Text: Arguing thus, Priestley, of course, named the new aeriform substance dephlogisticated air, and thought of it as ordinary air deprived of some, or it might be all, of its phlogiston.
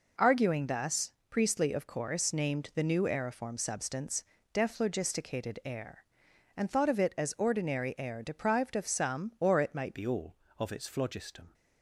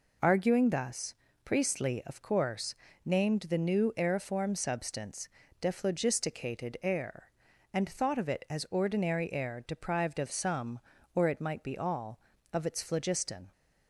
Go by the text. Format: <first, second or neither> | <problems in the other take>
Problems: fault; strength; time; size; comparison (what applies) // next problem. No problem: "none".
second | pauses between "substance" and "dephlogisticated"; slight; at 4.2 s; 0.30 s long; slight in the second // changes voice at "be"; from 9.9 s on; 1.6 s long